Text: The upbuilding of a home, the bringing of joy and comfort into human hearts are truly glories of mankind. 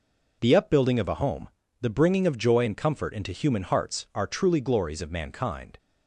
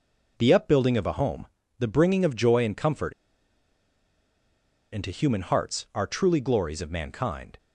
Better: first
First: none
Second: pauses between "comfort" and "into"; strong; at 3.1 s; 1.8 s long

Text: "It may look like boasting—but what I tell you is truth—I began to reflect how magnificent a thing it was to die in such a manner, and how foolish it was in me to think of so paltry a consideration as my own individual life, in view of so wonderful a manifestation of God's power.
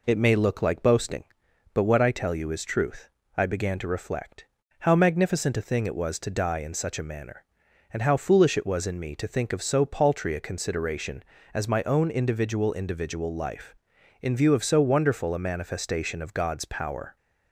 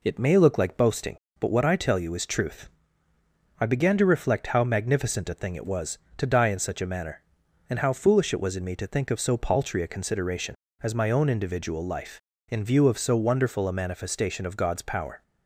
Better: second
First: pauses between "reflect" and "how"; slight; at 4.4 s; 0.34 s long // says "individual" twice; at 12.7 s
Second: none

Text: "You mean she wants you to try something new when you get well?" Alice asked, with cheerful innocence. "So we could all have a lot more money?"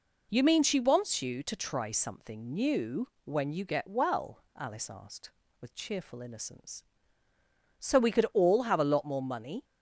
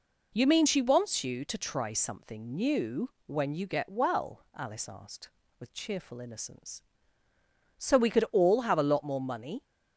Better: neither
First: pauses between "new" and "when"; slight; at 3.0 s; 0.16 s long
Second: pauses between "new" and "when"; slight; at 3.0 s; 0.16 s long

